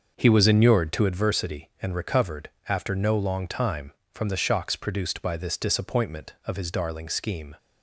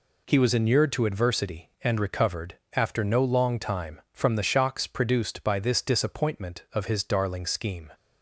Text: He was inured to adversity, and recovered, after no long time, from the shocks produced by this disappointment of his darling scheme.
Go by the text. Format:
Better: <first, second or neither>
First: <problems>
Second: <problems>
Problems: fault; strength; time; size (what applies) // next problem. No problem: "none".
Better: second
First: starts louder than the rest; until 1.1 s; 6 dB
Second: none